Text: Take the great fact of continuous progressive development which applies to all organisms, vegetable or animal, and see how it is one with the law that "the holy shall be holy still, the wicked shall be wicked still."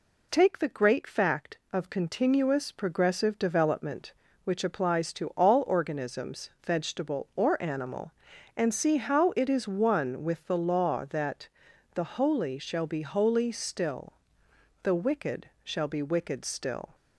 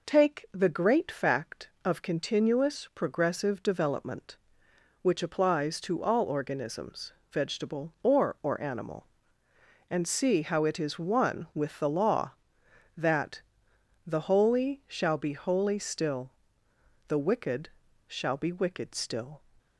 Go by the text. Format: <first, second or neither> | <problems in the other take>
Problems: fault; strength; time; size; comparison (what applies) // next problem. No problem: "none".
first | says "or" twice; at 8.4 s // pauses between "that" and "the"; noticeable; at 13.4 s; 0.64 s long; noticeable in the first // pauses between "wicked" and "shall"; slight; at 17.6 s; 0.36 s long; slight in the first